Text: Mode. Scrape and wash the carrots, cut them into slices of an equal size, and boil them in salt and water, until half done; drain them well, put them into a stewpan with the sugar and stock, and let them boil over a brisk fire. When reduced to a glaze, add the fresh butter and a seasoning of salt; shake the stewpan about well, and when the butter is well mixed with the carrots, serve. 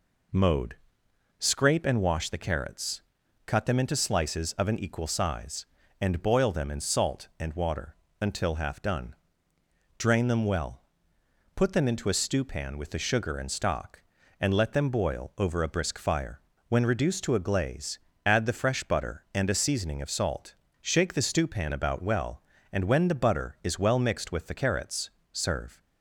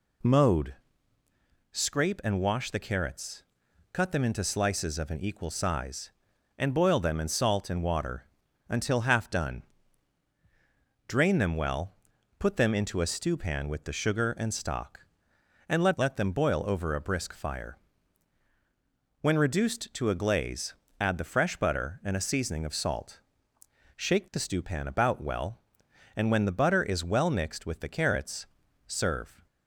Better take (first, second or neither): first